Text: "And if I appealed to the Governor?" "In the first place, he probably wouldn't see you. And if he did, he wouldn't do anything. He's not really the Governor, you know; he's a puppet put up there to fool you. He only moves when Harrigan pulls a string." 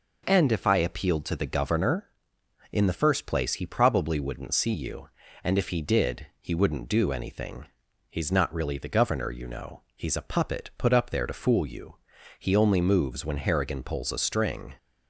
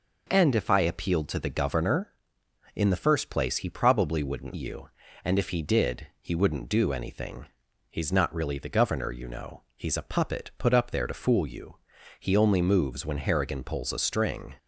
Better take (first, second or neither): first